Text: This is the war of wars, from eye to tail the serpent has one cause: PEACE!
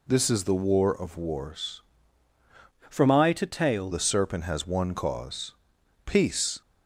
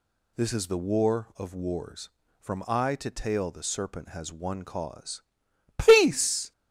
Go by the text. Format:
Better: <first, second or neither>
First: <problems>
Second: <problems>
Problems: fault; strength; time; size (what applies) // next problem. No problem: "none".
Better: second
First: changes voice from "from" to "tail"; from 2.8 to 3.9 s; 1.1 s long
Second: none